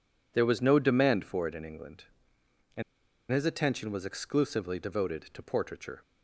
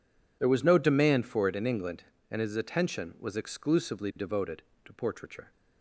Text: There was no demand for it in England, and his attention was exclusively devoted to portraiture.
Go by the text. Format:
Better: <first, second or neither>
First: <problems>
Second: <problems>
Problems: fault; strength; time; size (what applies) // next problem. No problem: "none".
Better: second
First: pauses between "and" and "his"; noticeable; at 2.8 s; 0.48 s long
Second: none